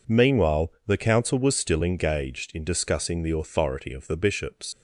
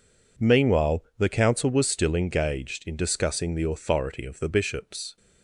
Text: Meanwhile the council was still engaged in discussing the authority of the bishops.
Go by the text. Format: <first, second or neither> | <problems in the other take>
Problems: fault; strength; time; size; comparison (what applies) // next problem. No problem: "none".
second | leaves "bishops" unfinished; at 4.7 s; 125 ms